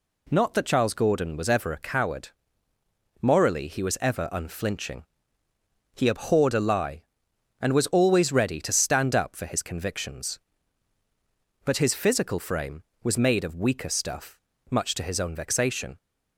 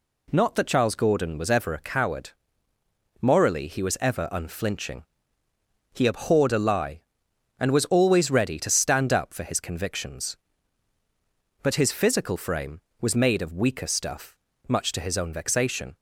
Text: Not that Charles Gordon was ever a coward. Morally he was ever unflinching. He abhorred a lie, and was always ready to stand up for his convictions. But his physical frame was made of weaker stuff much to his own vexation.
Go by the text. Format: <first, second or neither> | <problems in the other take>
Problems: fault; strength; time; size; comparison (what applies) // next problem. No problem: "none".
neither | pauses between "stuff" and "much"; slight; the same in both